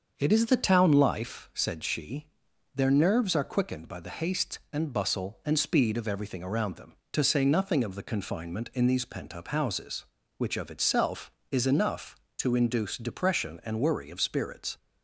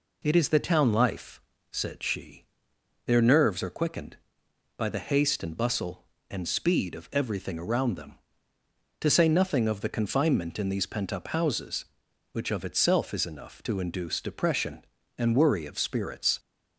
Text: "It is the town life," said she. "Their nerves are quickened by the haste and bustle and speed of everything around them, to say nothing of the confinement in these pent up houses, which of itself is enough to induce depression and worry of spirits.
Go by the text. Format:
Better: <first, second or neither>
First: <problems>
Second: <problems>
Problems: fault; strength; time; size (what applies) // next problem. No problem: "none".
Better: second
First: starts louder than the rest; until 1.8 s; 6.5 dB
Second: none